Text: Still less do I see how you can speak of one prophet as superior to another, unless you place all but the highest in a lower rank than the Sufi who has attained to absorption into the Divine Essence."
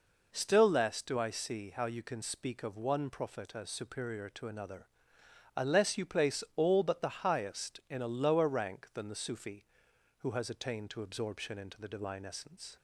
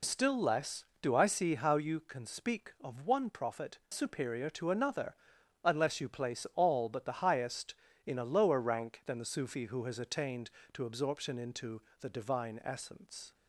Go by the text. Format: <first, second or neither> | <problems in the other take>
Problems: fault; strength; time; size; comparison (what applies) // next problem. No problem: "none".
first | skips "as"; at 3.8 s // pauses between "into" and "the"; slight; at 11.8 s; 0.18 s long